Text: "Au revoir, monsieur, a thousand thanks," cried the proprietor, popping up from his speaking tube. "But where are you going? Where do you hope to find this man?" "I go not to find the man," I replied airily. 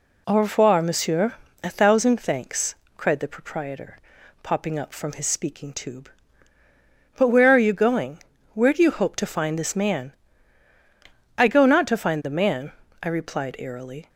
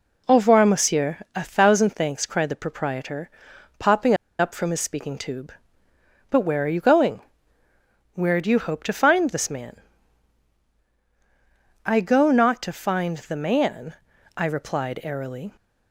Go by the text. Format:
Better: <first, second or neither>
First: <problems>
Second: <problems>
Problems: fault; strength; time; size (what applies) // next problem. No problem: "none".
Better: first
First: none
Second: pauses between "popping" and "up"; slight; at 4.1 s; 0.25 s long